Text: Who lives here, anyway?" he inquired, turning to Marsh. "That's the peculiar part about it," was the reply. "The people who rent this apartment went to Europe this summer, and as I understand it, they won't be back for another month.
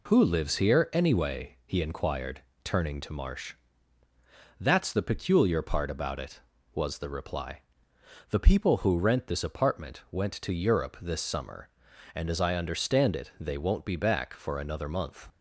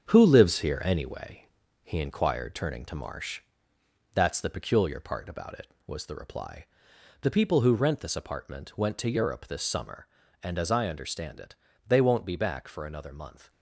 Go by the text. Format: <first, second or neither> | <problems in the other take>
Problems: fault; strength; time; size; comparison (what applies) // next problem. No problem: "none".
first | gets quieter; noticeable; throughout; 6 dB